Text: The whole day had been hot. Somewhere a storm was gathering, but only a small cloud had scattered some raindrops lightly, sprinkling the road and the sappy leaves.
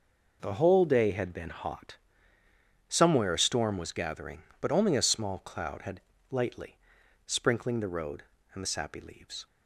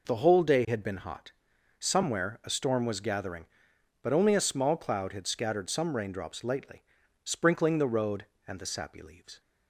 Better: second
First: skips "scattered some raindrops"; at 6.1 s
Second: none

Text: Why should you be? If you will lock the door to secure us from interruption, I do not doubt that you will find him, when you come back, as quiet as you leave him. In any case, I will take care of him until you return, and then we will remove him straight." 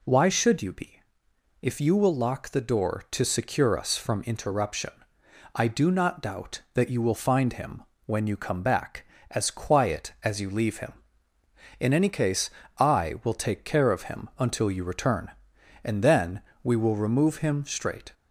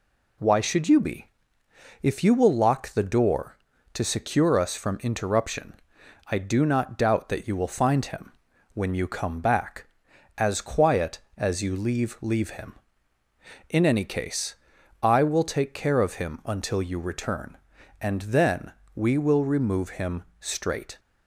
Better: first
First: pauses between "then" and "we"; slight; at 16.4 s; 0.24 s long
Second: says "leave" twice; at 12.2 s // pauses between "then" and "we"; slight; at 18.7 s; 0.24 s long // pauses between "him" and "straight"; slight; at 20.2 s; 0.16 s long

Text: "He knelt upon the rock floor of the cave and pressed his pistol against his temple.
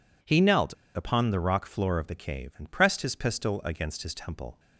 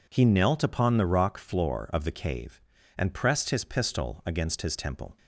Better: second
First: pauses between "knelt" and "upon"; slight; at 0.7 s; 0.22 s long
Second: none

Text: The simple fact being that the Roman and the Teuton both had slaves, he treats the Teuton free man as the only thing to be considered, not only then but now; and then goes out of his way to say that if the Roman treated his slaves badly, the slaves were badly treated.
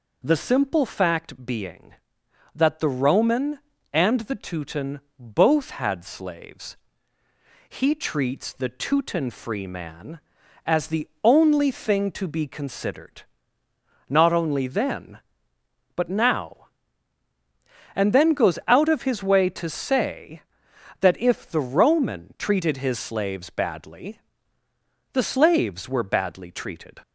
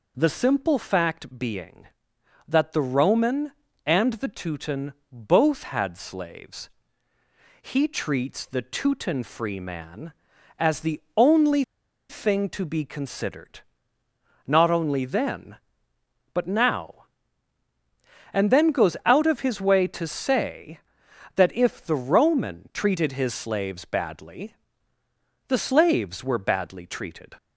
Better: first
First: pauses between "Teuton" and "both"; slight; at 4.9 s; 0.18 s long // pauses between "the" and "only"; slight; at 11.0 s; 0.16 s long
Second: pauses between "Teuton" and "both"; slight; at 4.9 s; 0.18 s long // pauses between "the" and "only"; slight; at 11.0 s; 0.16 s long // pauses between "only" and "thing"; at 11.6 s; 0.45 s long

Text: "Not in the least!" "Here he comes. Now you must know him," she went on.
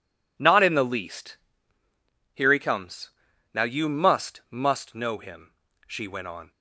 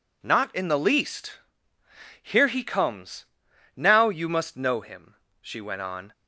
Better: second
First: says "must" twice; at 4.5 s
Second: none

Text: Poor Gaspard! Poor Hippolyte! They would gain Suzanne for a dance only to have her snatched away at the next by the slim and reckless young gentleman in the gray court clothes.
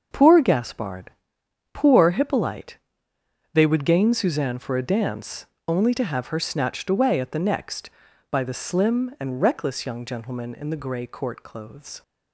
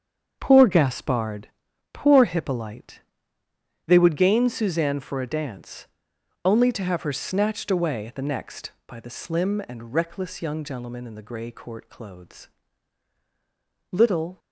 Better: first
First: starts louder than the rest; until 1.7 s; 6.5 dB // pauses between "dance" and "only"; slight; at 5.4 s; 0.20 s long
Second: starts louder than the rest; strong; until 1.4 s; 7.5 dB // pauses between "dance" and "only"; noticeable; at 5.8 s; 0.58 s long // goes on to say "Little"; slight; from 13.9 s on; 0.48 s long

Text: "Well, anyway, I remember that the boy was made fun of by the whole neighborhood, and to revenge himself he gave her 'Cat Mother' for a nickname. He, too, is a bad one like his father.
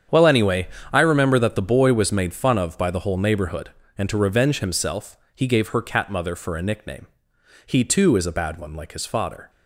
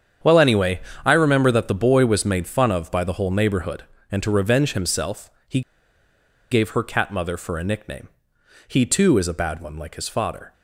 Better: first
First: starts louder than the rest; strong; until 1.3 s; 8.5 dB // pauses between "himself" and "he"; slight; at 5.1 s; 0.18 s long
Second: starts louder than the rest; strong; until 1.4 s; 8.5 dB // pauses between "himself" and "he"; slight; at 5.3 s; 0.18 s long // pauses between "he" and "gave"; noticeable; at 5.6 s; 0.91 s long

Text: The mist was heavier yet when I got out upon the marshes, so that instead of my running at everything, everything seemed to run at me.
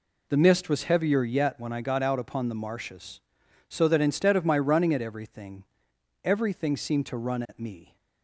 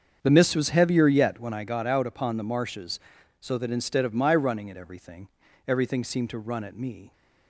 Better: first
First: none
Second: starts louder than the rest; strong; until 1.8 s; 7 dB

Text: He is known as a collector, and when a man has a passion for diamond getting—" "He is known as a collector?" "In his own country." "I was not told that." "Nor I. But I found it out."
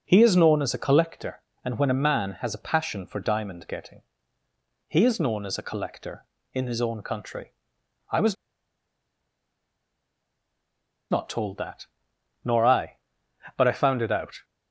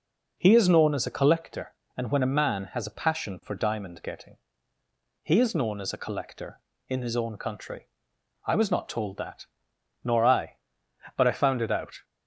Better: second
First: pauses between "was" and "not"; strong; at 8.3 s; 2.7 s long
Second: none

